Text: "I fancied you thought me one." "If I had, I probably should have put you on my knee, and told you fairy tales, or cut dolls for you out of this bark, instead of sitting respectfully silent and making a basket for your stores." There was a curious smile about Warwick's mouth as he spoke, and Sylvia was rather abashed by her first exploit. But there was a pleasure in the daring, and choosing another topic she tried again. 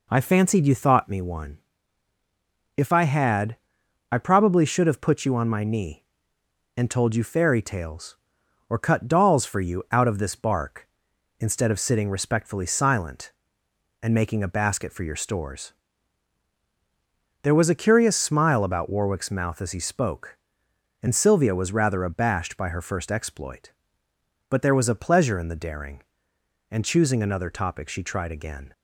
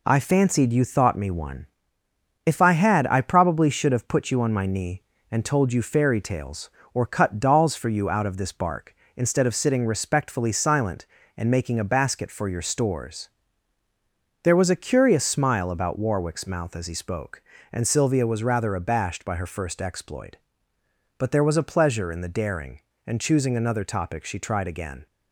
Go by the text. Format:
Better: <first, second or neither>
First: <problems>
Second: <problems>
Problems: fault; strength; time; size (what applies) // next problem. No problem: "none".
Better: neither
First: none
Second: none